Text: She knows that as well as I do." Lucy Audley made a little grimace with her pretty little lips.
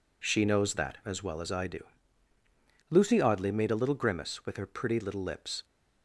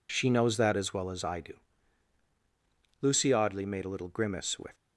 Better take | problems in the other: first | stops before "her pretty little lips"; at 4.7 s

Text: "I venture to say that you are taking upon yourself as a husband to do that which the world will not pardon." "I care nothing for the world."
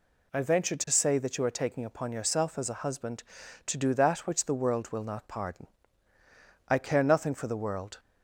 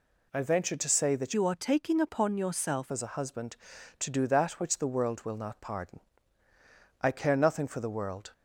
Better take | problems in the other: first | changes voice from "you" to "yourself"; from 1.3 to 2.9 s; 1.6 s long

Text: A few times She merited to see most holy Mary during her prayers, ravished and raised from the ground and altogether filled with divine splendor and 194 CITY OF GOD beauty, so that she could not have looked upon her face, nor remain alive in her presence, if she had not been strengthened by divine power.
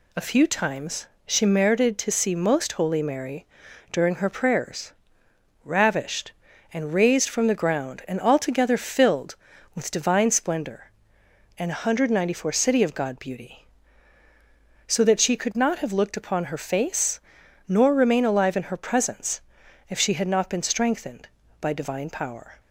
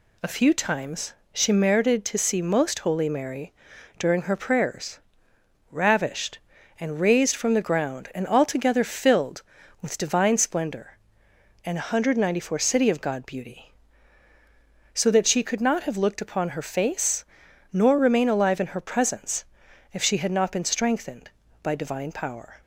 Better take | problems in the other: neither | pauses between "times" and "She"; slight; the same in both // pauses between "Mary" and "during"; noticeable; the same in both

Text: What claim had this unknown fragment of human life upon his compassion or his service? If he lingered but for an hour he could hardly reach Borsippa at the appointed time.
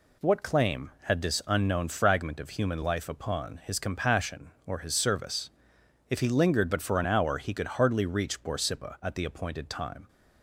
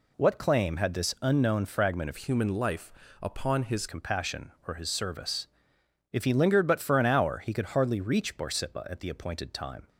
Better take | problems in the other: first | changes voice from "human" to "his"; from 2.1 to 3.8 s; 1.7 s long // pauses between "life" and "upon"; slight; at 2.9 s; 0.30 s long

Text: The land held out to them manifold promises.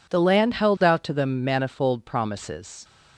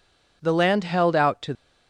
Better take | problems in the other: first | stops before "them manifold promises"; at 1.5 s

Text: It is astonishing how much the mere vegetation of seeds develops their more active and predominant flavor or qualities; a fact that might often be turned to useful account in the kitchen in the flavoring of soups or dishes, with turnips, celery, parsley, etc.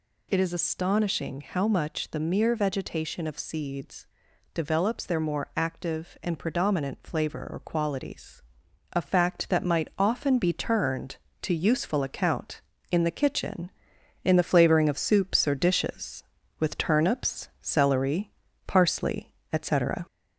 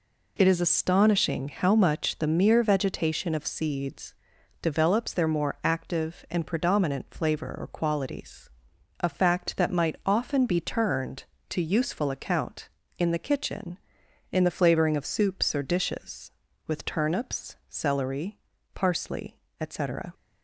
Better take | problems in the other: second | gets louder; slight; throughout; 2 dB // pauses between "seeds" and "develops"; noticeable; at 4.0 s; 0.48 s long; noticeable in the second

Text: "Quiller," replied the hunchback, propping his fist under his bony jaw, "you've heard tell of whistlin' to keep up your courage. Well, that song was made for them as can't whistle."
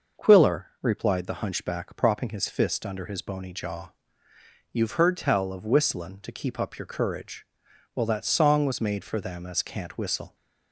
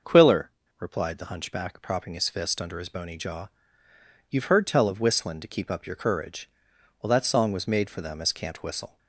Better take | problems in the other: neither | none

